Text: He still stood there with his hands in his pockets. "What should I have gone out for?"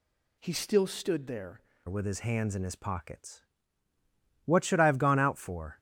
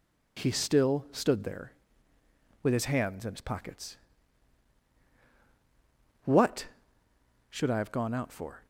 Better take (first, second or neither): second